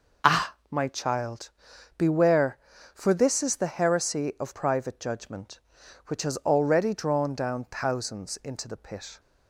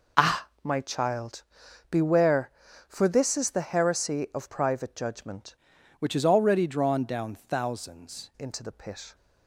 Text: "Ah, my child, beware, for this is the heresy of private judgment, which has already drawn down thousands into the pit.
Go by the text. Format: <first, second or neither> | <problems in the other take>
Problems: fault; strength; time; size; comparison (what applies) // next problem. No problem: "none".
first | changes voice from "which" to "thousands"; from 5.9 to 8.3 s; 2.4 s long